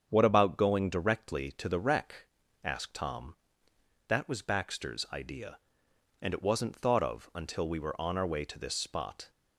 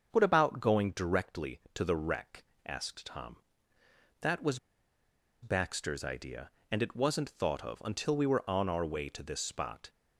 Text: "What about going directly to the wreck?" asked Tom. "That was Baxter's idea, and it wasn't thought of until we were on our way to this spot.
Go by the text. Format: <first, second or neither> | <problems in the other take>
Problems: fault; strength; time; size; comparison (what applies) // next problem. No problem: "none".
first | starts louder than the rest; until 1.1 s; 7 dB; strong in the first // pauses between "was" and "Baxter's"; noticeable; at 4.5 s; 0.84 s long